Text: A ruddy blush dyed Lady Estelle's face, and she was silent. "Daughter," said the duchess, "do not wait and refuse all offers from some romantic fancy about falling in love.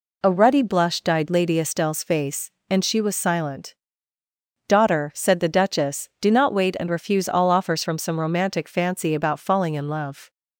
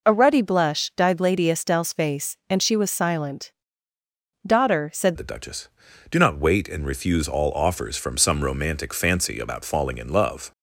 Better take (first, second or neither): first